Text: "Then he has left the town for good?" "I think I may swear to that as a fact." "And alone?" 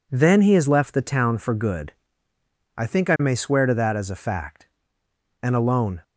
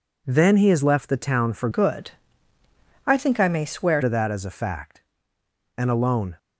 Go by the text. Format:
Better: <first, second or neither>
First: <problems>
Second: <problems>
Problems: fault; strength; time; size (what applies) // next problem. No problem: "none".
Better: first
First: none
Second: changes voice from "good" to "swear"; from 1.7 to 4.0 s; 2.3 s long